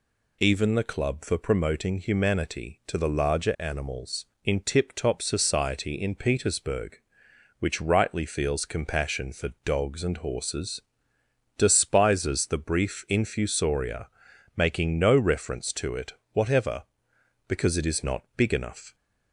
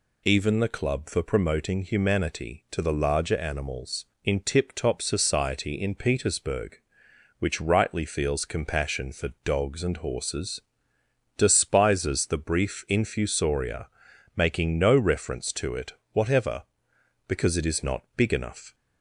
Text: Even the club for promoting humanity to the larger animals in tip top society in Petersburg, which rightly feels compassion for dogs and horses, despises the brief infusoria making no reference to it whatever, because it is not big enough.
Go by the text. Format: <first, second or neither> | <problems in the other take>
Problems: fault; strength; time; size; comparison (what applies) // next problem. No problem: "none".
neither | pauses between "for" and "dogs"; slight; the same in both // pauses between "infusoria" and "making"; noticeable; the same in both // pauses between "it" and "whatever"; slight; the same in both